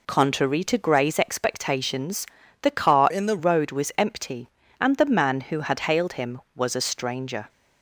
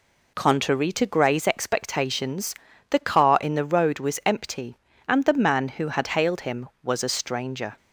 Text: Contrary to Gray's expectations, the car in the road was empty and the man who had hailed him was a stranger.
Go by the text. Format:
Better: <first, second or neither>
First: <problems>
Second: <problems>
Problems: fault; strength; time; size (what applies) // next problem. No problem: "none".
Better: second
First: changes voice from "in" to "the"; from 3.0 to 3.3 s; 0.3 s long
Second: none